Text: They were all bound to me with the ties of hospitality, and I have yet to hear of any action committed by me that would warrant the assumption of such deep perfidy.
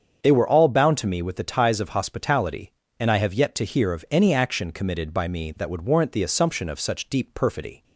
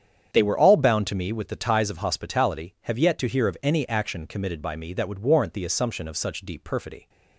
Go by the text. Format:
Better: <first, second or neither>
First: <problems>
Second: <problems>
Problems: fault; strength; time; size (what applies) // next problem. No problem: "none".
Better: first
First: starts louder than the rest; strong; until 1.2 s; 7.5 dB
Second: starts louder than the rest; strong; until 1.3 s; 8.5 dB // skips "and I"; at 2.7 s